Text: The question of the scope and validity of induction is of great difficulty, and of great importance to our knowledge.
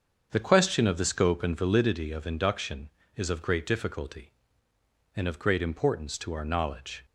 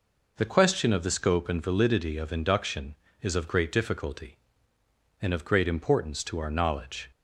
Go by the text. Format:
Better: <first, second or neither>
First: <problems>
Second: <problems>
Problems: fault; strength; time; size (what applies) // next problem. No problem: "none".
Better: second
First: starts louder than the rest; strong; until 1.9 s; 7 dB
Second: none